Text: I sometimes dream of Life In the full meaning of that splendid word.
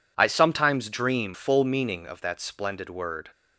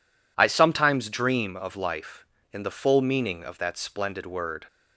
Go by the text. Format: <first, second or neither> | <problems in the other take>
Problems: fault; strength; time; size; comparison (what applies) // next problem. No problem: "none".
second | skips "of Life In the"; at 1.3 s